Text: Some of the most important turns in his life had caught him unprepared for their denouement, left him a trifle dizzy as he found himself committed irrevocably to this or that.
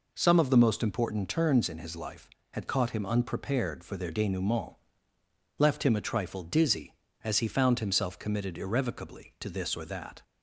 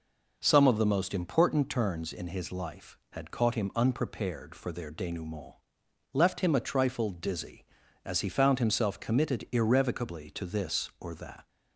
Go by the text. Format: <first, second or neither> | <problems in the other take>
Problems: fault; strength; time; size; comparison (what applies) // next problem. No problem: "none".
neither | none